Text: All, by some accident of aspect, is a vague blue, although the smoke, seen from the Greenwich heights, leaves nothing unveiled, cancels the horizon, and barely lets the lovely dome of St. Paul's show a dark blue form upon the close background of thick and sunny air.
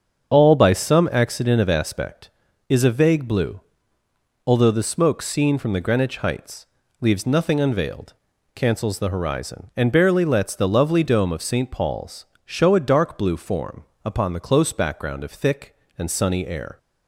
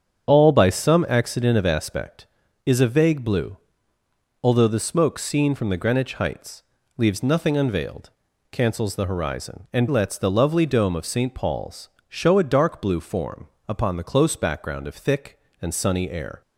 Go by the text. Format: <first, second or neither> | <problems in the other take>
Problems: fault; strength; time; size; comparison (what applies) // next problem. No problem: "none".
first | starts louder than the rest; strong; until 1.3 s; 8 dB; also in the first // skips "barely"; at 9.8 s // pauses between "Paul's" and "show"; slight; at 11.8 s; 0.22 s long; slight in the first // pauses between "form" and "upon"; slight; at 13.4 s; 0.22 s long; slight in the first